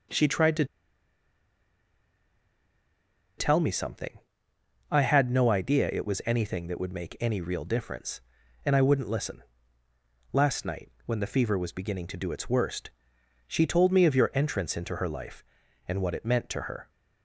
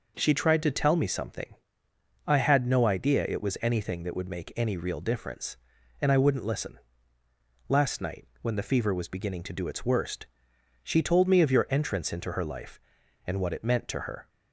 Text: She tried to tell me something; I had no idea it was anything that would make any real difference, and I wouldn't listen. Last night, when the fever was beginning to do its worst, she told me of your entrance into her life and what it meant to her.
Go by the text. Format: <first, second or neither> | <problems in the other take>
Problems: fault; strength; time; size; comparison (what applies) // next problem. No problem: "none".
second | pauses between "to" and "tell"; strong; at 0.6 s; 2.7 s long